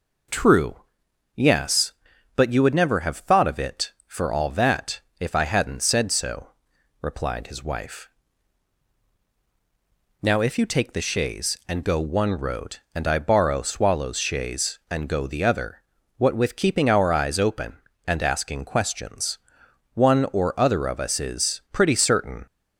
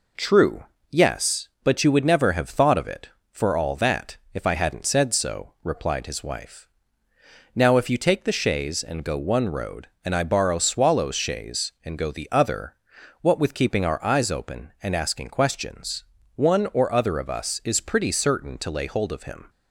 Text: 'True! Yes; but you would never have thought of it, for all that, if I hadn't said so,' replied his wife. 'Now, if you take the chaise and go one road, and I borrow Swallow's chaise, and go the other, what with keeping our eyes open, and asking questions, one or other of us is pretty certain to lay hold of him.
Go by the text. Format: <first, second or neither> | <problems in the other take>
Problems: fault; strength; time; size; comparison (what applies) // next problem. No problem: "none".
second | stops before "to lay hold of him"; at 22.4 s